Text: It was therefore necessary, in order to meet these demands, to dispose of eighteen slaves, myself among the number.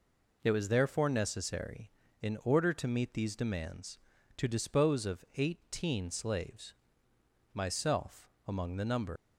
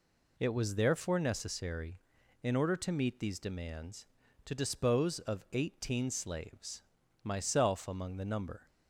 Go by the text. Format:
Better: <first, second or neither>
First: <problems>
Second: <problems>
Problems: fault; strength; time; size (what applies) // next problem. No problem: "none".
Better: second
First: pauses between "myself" and "among"; slight; at 8.2 s; 0.20 s long // leaves "number" unfinished; at 9.1 s; 100 ms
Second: none